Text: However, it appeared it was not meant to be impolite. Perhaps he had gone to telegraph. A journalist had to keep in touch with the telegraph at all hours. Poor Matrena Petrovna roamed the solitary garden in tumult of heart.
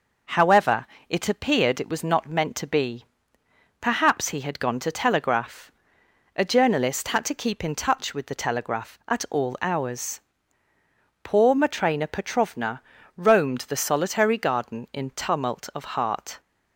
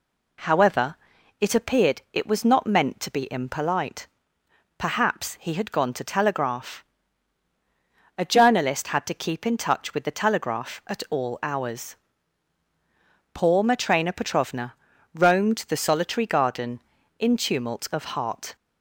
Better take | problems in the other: second | skips "impolite"; at 3.4 s // pauses between "Petrovna" and "roamed"; slight; at 12.8 s; 0.36 s long; also in the second

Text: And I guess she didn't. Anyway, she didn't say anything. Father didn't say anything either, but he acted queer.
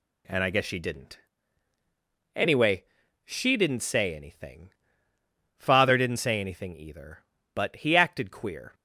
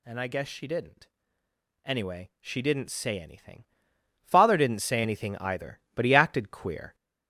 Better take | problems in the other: first | gets louder; noticeable; throughout; 4.5 dB

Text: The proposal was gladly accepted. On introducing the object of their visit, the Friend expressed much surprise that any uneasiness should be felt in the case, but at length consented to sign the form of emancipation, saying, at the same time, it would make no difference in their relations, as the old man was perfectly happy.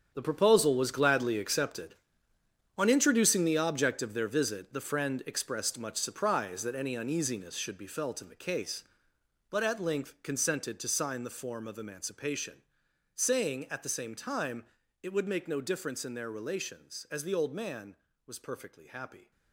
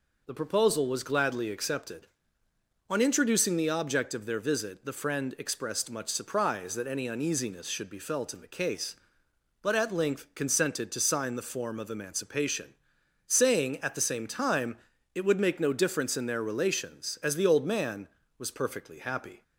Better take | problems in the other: second | gets quieter; strong; throughout; 12.5 dB

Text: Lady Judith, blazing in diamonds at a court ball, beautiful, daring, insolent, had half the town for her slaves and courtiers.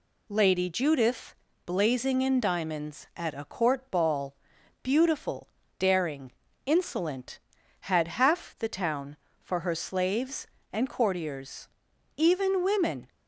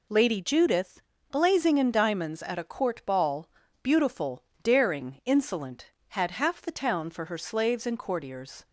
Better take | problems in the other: second | goes on to say "Even women"; noticeable; from 12.1 s on; 0.90 s long

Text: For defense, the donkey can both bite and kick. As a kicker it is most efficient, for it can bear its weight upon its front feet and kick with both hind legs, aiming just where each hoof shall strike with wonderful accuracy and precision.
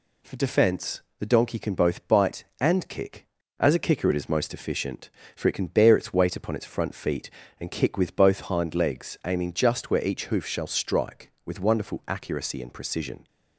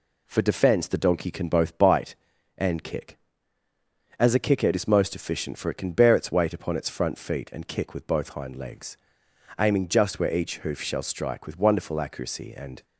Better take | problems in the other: first | stops before "precision"; at 12.8 s

